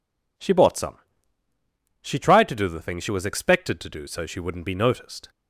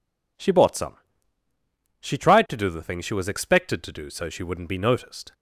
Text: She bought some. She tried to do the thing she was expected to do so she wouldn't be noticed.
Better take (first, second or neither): neither